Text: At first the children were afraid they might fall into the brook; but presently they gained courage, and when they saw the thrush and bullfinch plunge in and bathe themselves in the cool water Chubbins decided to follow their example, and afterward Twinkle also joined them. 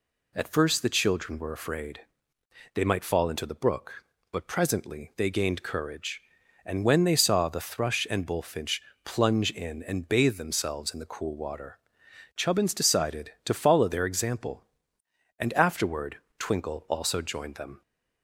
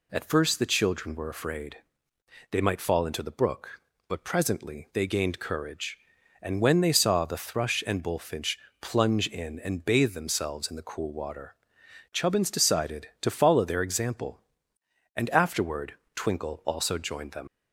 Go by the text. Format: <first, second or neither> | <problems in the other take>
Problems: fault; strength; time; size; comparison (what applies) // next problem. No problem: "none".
first | pauses between "afraid" and "they"; noticeable; at 1.7 s; 0.74 s long; noticeable in the first // pauses between "bullfinch" and "plunge"; slight; at 8.5 s; 0.22 s long; slight in the first // pauses between "water" and "Chubbins"; noticeable; at 11.5 s; 0.58 s long; noticeable in the first // pauses between "afterward" and "Twinkle"; slight; at 15.9 s; 0.22 s long; slight in the first // leaves "them" unfinished; at 17.4 s; 110 ms